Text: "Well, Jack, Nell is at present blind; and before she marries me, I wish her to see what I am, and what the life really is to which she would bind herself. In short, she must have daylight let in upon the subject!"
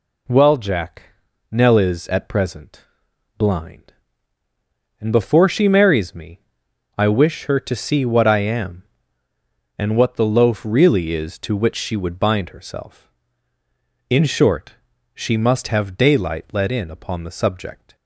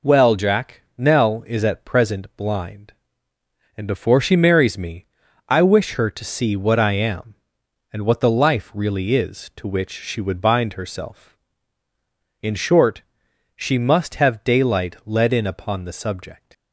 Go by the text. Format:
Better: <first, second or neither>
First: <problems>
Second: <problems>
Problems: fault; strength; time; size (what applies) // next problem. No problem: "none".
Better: second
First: pauses between "present" and "blind"; noticeable; at 2.8 s; 0.52 s long // says "loaf" for "life"; at 10.2 s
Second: none